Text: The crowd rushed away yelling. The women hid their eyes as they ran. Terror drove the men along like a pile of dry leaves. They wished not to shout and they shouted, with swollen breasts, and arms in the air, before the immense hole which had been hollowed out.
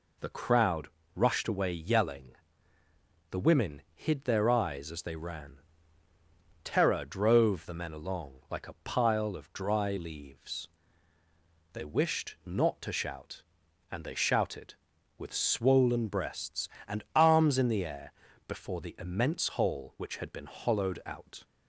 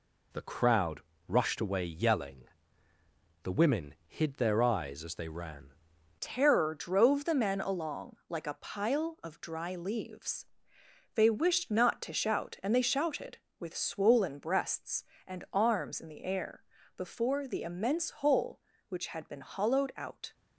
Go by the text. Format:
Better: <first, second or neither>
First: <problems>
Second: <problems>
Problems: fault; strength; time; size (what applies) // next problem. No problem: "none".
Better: first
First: pauses between "crowd" and "rushed"; slight; at 0.8 s; 0.26 s long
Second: pauses between "crowd" and "rushed"; slight; at 1.0 s; 0.26 s long // changes voice at "Terror"; from 6.1 s on; 14.2 s long